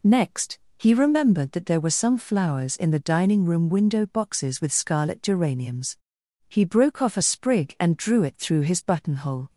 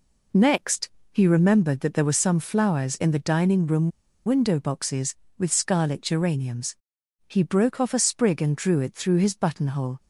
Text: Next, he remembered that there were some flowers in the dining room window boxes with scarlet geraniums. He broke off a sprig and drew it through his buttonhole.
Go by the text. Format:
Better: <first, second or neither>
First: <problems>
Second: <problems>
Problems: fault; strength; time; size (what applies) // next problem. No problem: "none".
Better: first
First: none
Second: pauses between "room" and "window"; slight; at 3.9 s; 0.35 s long